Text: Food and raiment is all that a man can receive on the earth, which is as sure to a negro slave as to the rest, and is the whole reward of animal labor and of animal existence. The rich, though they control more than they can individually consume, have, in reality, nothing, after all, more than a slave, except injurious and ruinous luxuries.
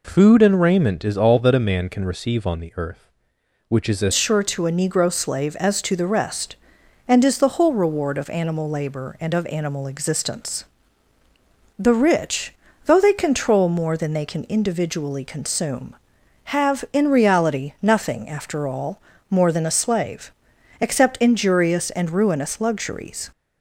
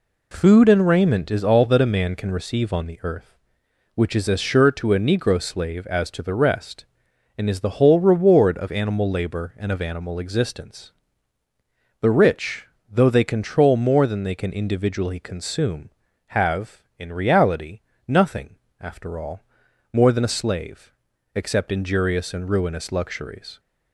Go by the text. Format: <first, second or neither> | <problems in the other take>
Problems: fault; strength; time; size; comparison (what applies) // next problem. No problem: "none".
second | changes voice at "sure"; from 4.1 s on; 19.1 s long